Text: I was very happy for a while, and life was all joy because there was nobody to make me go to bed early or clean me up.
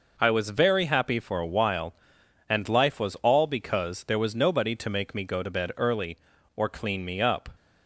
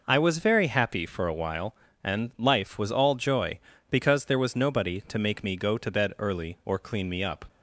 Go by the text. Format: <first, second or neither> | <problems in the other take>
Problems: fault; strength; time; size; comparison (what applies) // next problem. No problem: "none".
second | skips "joy"; at 3.4 s